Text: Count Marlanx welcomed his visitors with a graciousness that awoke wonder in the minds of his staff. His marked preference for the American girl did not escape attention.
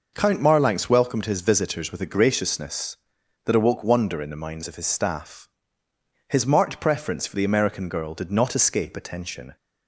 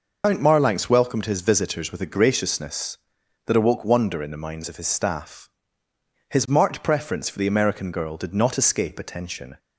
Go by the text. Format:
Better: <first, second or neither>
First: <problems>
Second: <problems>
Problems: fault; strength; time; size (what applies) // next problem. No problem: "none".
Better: first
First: none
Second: loses the start of "Count"; at 0.2 s; 100 ms